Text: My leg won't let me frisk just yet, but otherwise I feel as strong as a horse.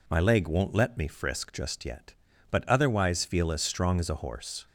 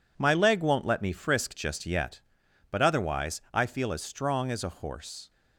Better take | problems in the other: second | skips "I"; at 3.2 s

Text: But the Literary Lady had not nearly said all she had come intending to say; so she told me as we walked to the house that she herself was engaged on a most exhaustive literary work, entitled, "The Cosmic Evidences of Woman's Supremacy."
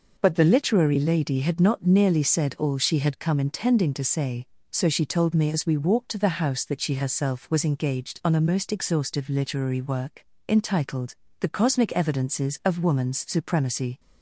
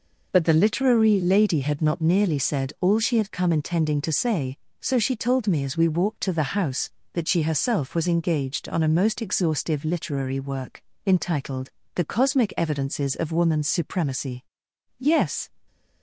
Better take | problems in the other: first | goes on to say "Yes"; slight; from 14.9 s on; 0.48 s long

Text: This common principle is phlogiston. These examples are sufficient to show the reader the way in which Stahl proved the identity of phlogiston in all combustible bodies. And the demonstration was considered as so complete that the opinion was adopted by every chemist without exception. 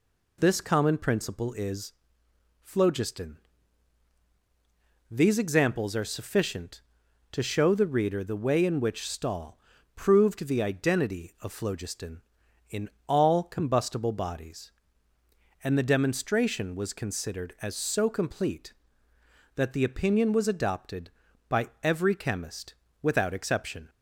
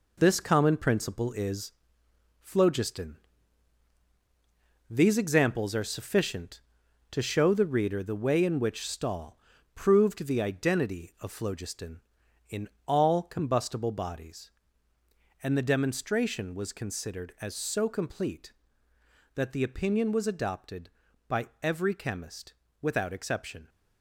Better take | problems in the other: first | gets quieter; throughout; 7 dB // pauses between "is" and "phlogiston"; noticeable; at 1.7 s; 0.72 s long; noticeable in the first // pauses between "Stahl" and "proved"; at 9.3 s; 0.38 s long; also in the first // pauses between "in" and "all"; slight; at 12.6 s; 0.18 s long; slight in the first // pauses between "by" and "every"; slight; at 21.4 s; 0.16 s long; slight in the first // pauses between "chemist" and "without"; slight; at 22.5 s; 0.28 s long; slight in the first

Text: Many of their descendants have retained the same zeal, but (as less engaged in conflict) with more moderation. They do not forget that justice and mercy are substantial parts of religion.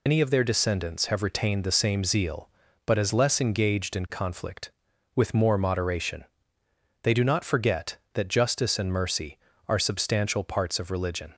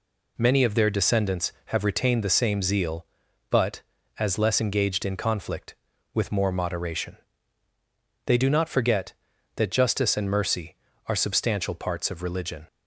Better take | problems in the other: second | loses the start of "Many"; at 0.0 s; 140 ms

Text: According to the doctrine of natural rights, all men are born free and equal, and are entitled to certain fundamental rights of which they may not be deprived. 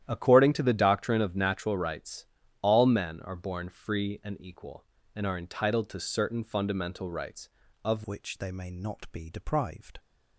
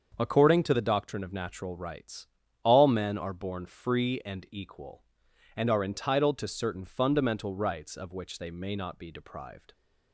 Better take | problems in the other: second | starts louder than the rest; strong; until 1.1 s; 11 dB; also in the second // changes voice at "which"; from 8.0 s on; 1.9 s long

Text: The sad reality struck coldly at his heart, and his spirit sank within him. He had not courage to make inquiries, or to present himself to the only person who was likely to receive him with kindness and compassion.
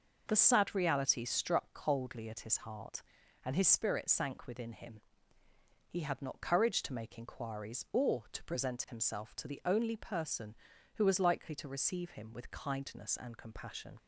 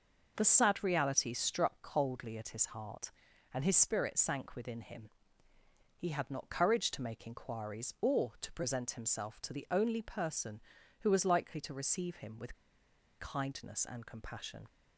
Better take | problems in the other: first | pauses between "with" and "kindness"; noticeable; at 12.5 s; 0.65 s long

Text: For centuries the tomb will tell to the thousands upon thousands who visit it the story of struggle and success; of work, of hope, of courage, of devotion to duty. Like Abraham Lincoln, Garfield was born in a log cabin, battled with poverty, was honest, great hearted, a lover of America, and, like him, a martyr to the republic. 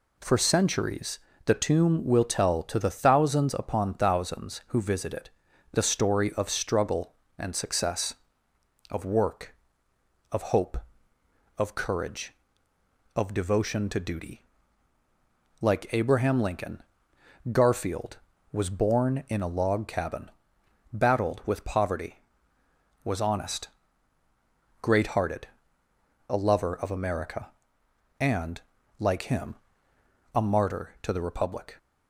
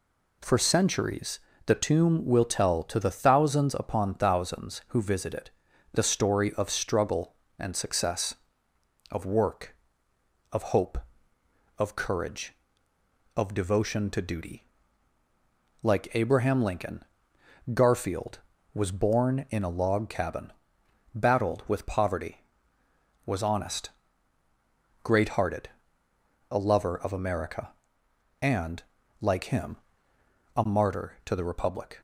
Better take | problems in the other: neither | pauses between "centuries" and "the"; slight; the same in both // pauses between "it" and "the"; the same in both

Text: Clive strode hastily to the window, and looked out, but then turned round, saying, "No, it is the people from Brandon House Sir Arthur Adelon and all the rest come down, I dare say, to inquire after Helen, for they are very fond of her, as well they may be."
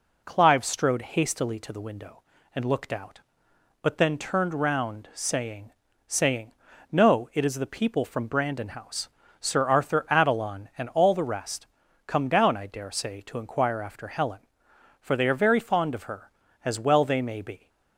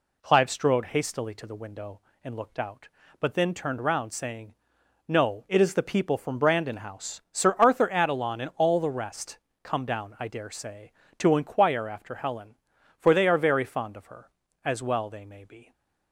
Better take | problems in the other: second | says "saying" twice; at 6.0 s // pauses between "House" and "Sir"; slight; at 9.0 s; 0.32 s long // pauses between "rest" and "come"; at 11.6 s; 0.40 s long; slight in the second

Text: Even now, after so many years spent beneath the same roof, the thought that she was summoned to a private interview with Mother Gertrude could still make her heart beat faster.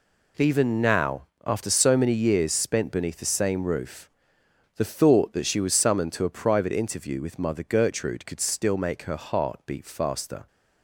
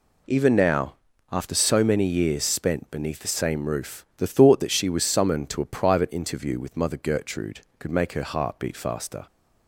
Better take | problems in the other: first | skips "still"; at 7.8 s

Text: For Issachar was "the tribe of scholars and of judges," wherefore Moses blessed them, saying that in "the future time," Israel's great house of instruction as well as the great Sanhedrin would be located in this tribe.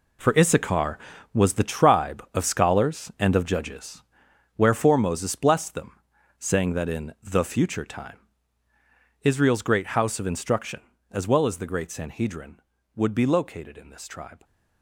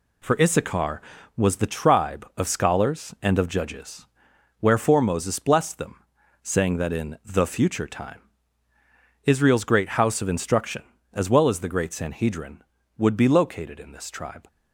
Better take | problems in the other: second | gets quieter; strong; throughout; 11 dB

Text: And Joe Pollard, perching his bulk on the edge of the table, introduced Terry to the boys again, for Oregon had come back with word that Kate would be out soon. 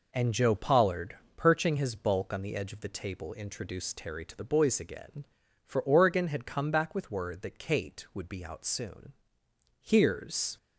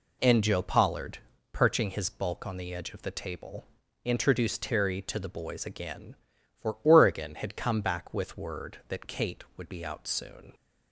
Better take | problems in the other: second | goes on to say "Here's"; noticeable; from 9.8 s on; 0.74 s long

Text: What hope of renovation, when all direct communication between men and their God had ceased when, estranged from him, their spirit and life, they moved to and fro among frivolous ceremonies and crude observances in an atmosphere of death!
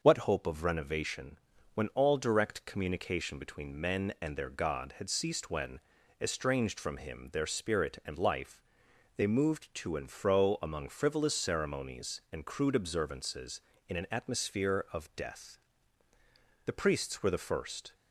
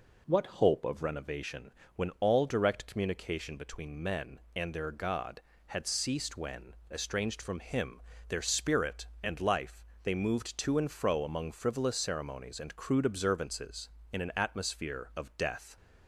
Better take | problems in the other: second | goes on to say "The priests were the first"; noticeable; from 16.6 s on; 1.2 s long

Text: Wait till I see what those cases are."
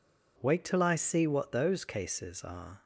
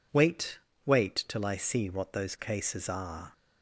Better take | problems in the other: first | says "Wait" twice; at 0.8 s

